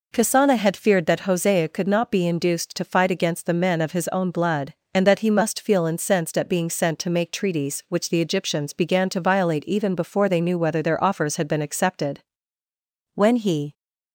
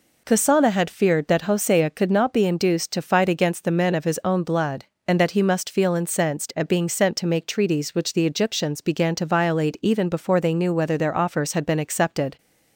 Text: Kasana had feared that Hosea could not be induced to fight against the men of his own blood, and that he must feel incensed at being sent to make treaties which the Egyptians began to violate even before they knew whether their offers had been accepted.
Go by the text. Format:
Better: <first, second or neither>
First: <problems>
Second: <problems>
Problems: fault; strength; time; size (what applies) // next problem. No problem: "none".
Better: second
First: goes on to say "When he"; from 13.1 s on; 0.58 s long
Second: none